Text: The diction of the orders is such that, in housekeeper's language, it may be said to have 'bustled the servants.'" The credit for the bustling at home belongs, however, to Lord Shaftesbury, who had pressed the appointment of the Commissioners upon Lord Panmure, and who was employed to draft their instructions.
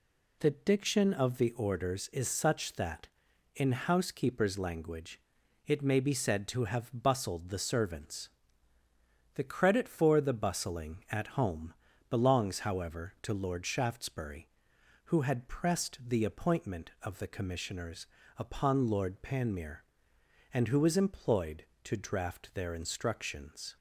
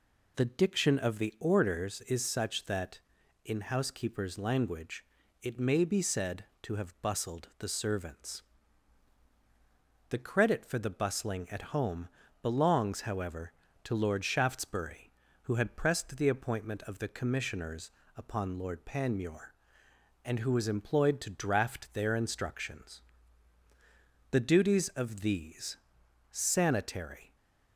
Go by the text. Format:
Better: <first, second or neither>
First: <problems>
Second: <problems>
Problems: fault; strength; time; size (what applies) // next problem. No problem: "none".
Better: first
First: pauses between "home" and "belongs"; at 11.7 s; 0.38 s long // pauses between "Commissioners" and "upon"; slight; at 18.0 s; 0.30 s long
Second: pauses between "home" and "belongs"; slight; at 12.0 s; 0.32 s long // pauses between "Commissioners" and "upon"; slight; at 17.8 s; 0.28 s long // goes on to say "The duties of these Sanitary"; strong; from 24.3 s on; 3.0 s long